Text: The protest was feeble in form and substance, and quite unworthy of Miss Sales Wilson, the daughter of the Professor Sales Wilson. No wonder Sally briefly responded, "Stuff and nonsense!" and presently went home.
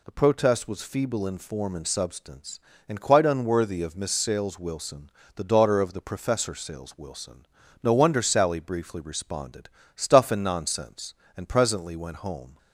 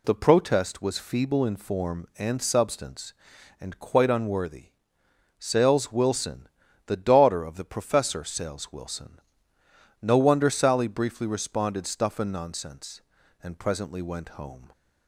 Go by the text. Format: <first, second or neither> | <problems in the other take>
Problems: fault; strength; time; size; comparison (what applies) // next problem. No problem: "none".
first | skips "of Miss"; at 5.0 s